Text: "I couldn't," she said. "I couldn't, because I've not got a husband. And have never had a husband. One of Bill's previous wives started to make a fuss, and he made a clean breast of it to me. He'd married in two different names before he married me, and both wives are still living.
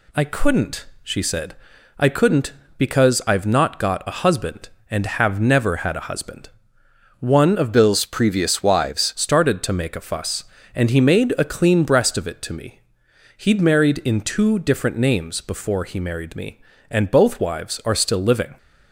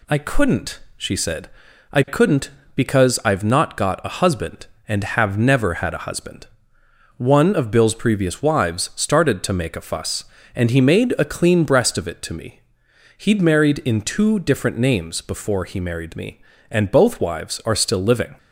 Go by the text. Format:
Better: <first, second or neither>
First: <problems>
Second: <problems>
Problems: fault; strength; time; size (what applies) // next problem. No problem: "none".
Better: second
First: changes voice from "Bill's" to "wives"; from 7.7 to 9.1 s; 1.4 s long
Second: none